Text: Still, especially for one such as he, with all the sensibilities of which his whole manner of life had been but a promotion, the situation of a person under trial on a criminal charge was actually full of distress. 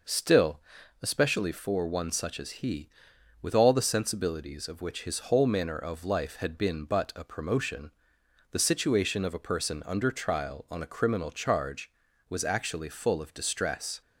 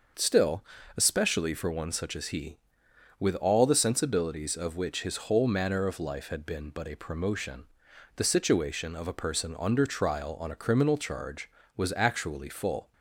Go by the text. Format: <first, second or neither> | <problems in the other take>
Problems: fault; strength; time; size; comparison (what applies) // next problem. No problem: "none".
first | starts louder than the rest; noticeable; until 1.5 s; 6 dB // stops before "of distress"; at 12.9 s